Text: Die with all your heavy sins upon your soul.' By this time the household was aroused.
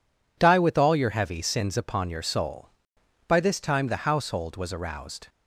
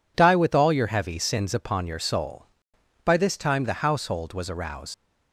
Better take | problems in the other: first | leaves "aroused" unfinished; at 4.9 s; 110 ms

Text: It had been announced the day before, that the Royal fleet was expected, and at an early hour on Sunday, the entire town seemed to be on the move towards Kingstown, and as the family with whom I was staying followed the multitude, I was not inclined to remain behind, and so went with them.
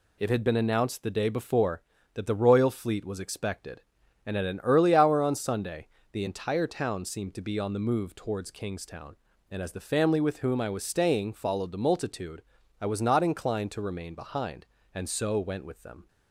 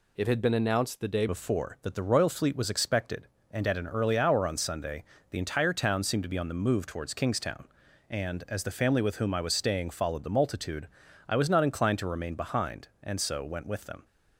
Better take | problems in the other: first | changes voice at "before"; from 1.2 s on; 12.8 s long

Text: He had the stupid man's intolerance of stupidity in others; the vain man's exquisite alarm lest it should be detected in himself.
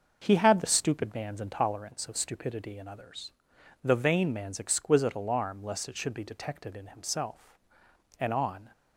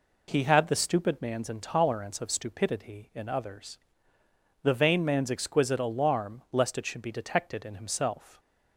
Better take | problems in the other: second | starts louder than the rest; until 1.2 s; 6 dB // goes on to say "And on"; slight; from 8.2 s on; 0.48 s long

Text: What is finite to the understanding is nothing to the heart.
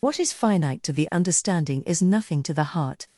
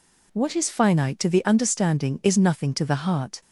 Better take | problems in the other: second | loses the start of "What"; at 0.0 s; 65 ms

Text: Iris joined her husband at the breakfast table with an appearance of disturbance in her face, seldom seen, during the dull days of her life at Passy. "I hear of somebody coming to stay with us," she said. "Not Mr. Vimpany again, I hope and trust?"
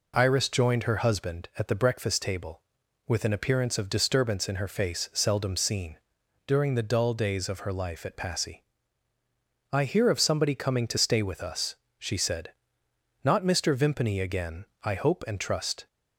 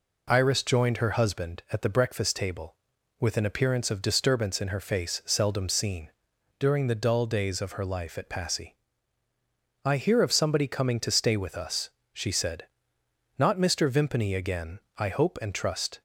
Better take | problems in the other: neither | none

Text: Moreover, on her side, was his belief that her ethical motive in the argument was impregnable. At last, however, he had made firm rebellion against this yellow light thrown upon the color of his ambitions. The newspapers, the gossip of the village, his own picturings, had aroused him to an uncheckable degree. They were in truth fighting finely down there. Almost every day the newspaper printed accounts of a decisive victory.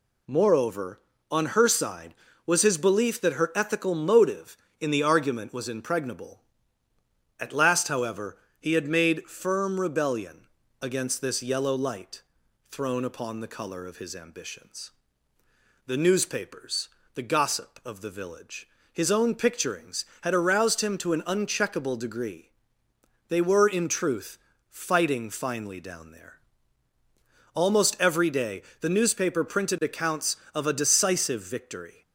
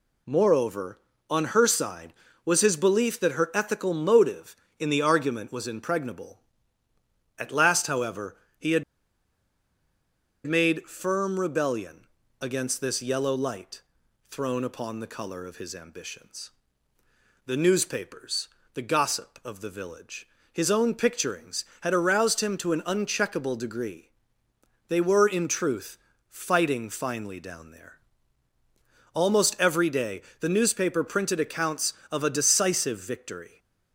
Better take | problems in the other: first | pauses between "had" and "made"; strong; at 8.8 s; 1.6 s long // pauses between "rebellion" and "against"; slight; at 12.0 s; 0.34 s long; slight in the first // pauses between "light" and "thrown"; noticeable; at 13.8 s; 0.48 s long; noticeable in the first // pauses between "truth" and "fighting"; slight; at 25.9 s; 0.32 s long; slight in the first // pauses between "day" and "the"; slight; at 30.2 s; 0.18 s long; slight in the first

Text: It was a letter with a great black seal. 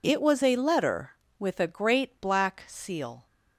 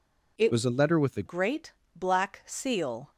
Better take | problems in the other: first | changes voice from "was" to "a"; from 0.5 to 1.2 s; 0.7 s long // pauses between "great" and "black"; slight; at 1.7 s; 0.24 s long

